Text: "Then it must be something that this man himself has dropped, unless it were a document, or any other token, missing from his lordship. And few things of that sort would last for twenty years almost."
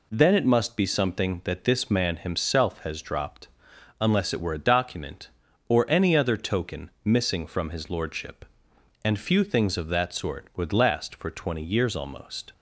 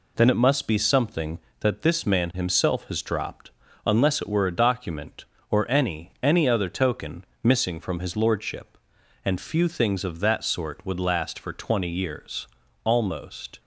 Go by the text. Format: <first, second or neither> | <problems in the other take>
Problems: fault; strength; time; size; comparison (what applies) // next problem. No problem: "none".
first | says "any" twice; at 6.2 s // pauses between "years" and "almost"; slight; at 12.4 s; 0.36 s long